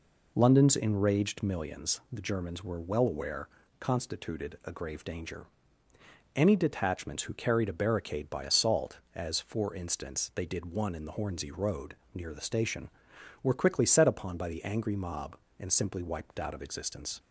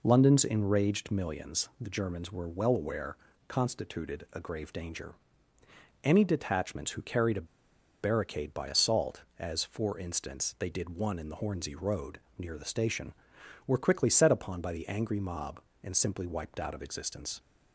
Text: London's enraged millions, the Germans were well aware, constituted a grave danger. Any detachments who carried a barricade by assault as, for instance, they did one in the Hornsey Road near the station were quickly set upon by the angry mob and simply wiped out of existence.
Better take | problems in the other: first | pauses between "a" and "barricade"; noticeable; at 7.4 s; 0.56 s long // pauses between "Road" and "near"; slight; at 12.1 s; 0.22 s long; slight in the first

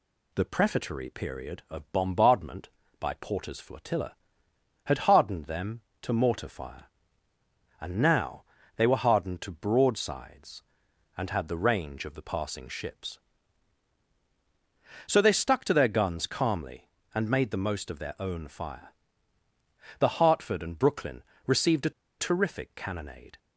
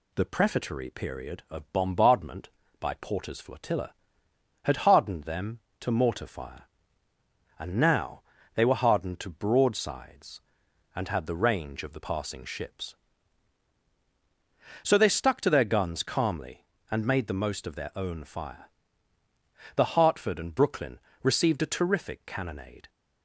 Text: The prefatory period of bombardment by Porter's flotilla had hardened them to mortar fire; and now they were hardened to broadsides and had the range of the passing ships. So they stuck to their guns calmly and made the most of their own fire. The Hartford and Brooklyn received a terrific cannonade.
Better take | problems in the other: second | pauses between "now" and "they"; slight; at 8.4 s; 0.32 s long; slight in the second // pauses between "Brooklyn" and "received"; slight; at 21.2 s; 0.22 s long; slight in the second // pauses between "a" and "terrific"; slight; at 21.9 s; 0.28 s long

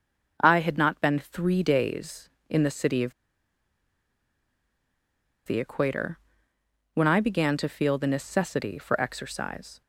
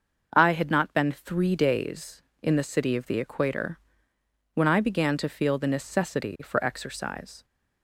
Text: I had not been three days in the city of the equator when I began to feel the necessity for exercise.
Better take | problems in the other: second | starts louder than the rest; until 1.4 s; 6 dB; also in the second // pauses between "of" and "the"; strong; at 3.1 s; 2.3 s long // pauses between "equator" and "when"; noticeable; at 6.1 s; 0.74 s long; noticeable in the second

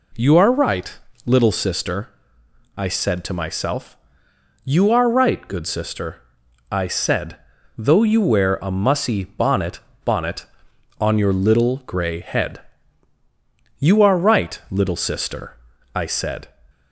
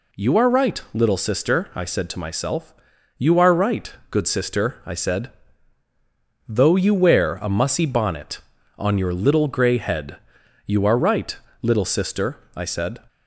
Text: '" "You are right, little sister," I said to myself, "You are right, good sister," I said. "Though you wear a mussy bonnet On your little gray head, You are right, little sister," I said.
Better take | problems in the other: second | says "bonnet" twice; at 10.0 s

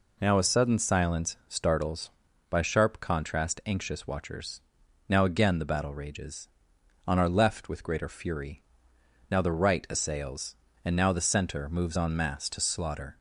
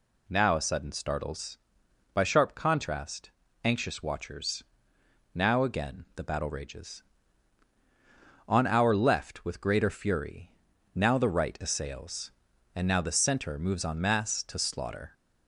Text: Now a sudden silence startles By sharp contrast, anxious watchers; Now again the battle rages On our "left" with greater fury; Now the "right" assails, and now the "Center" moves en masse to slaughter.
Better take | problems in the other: first | skips "silence"; at 0.9 s

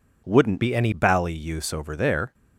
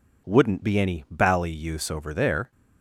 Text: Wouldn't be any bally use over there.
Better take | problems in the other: second | changes voice from "be" to "any"; from 0.6 to 0.9 s; 0.3 s long

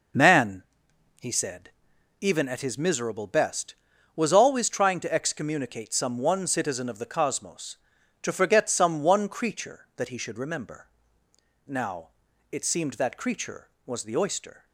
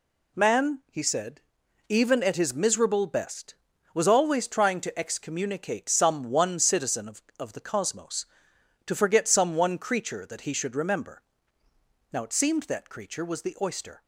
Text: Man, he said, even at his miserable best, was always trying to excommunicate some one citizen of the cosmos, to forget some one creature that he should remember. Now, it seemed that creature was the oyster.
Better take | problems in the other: first | says "of" twice; at 7.3 s

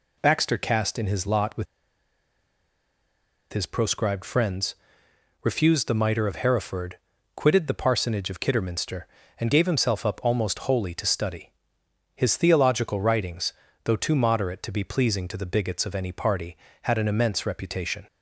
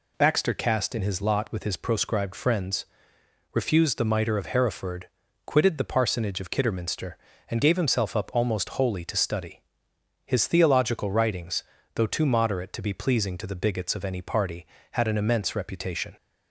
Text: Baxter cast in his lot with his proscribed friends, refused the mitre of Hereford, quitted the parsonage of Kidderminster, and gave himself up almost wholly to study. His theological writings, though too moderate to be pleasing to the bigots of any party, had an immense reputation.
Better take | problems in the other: second | pauses between "with" and "his"; strong; at 1.6 s; 1.8 s long

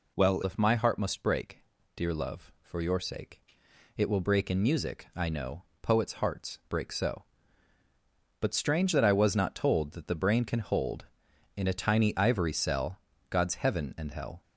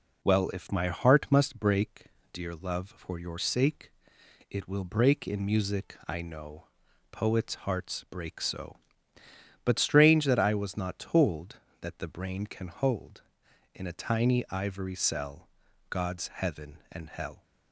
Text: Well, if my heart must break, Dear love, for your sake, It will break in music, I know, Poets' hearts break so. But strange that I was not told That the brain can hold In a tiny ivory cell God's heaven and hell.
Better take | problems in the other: second | changes voice at "if"; from 0.4 s on; 14.0 s long // pauses between "cell" and "God's"; slight; at 12.9 s; 0.32 s long; also in the second

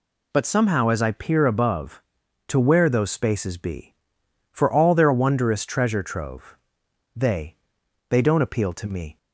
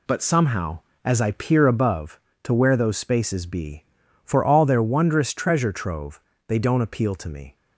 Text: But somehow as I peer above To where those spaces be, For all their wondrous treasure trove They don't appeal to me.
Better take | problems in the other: second | pauses between "trove" and "They"; noticeable; at 6.5 s; 0.60 s long; slight in the second // says "They" twice; at 8.0 s

